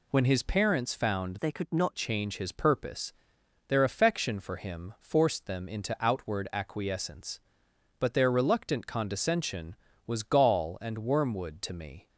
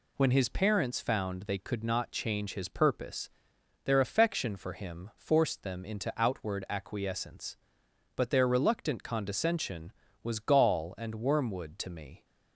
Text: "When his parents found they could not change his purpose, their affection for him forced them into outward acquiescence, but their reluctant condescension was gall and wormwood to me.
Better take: second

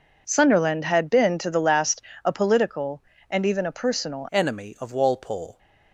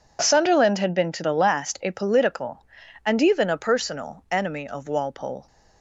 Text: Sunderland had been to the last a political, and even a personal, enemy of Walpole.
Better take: second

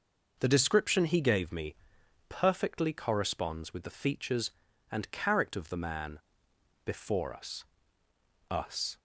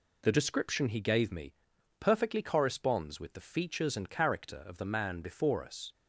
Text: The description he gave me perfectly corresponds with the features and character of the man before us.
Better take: second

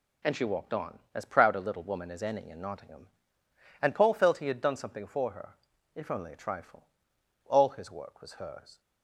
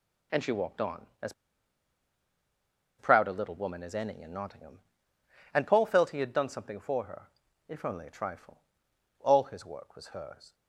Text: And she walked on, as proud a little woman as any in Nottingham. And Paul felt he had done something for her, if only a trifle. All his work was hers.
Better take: first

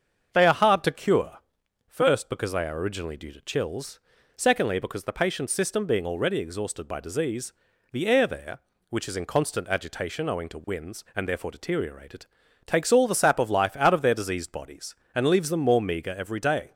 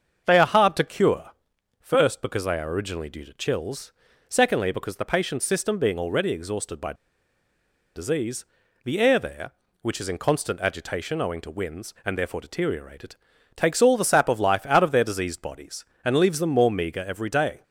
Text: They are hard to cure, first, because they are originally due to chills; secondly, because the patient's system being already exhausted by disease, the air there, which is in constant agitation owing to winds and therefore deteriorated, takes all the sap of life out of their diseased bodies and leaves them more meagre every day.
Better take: first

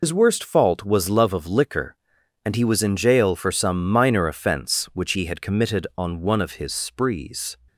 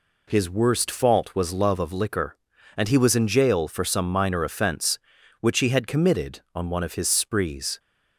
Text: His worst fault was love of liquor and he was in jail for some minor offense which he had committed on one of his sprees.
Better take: second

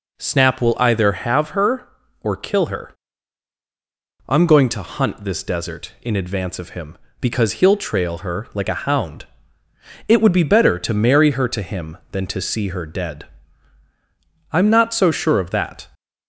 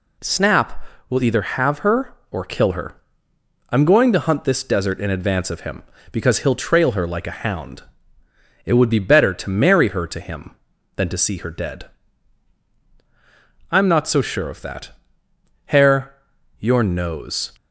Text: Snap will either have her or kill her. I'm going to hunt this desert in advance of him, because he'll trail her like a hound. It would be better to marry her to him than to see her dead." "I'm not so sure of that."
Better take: first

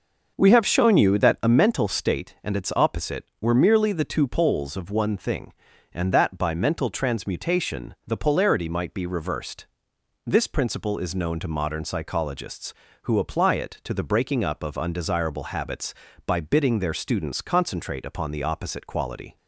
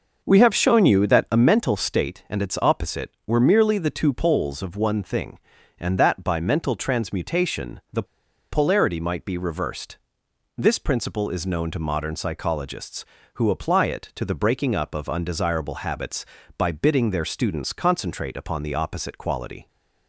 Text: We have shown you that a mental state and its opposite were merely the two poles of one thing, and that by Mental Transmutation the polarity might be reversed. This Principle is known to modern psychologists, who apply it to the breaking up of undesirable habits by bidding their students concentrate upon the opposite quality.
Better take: first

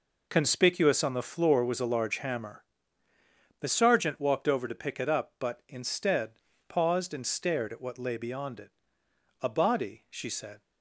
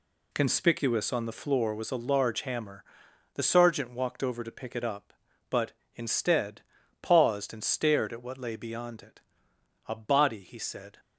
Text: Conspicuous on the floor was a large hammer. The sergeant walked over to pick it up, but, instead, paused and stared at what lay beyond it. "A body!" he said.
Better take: second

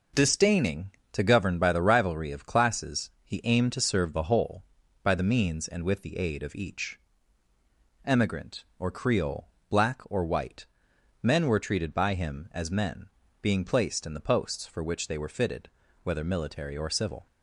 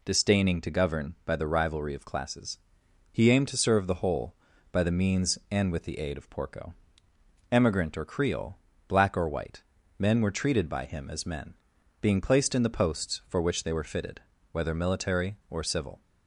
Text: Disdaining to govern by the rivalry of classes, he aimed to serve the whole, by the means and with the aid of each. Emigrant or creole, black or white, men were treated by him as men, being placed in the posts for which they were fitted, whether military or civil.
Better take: first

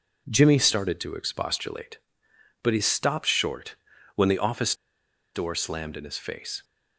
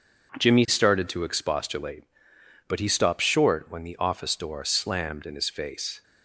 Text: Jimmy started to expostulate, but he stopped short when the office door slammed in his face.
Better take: second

